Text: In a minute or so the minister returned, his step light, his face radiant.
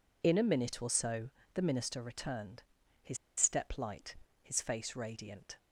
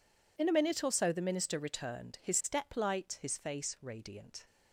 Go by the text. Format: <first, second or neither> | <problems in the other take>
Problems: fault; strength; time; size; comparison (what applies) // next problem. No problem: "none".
second | pauses between "so" and "the"; slight; at 1.2 s; 0.24 s long // pauses between "his" and "step"; slight; at 3.1 s; 0.22 s long